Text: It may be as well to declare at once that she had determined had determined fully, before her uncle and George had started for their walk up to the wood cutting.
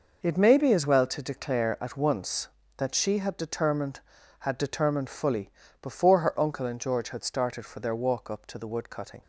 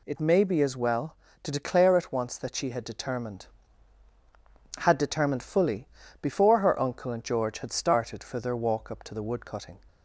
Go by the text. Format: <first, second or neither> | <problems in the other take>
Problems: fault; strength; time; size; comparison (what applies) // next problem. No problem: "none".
neither | none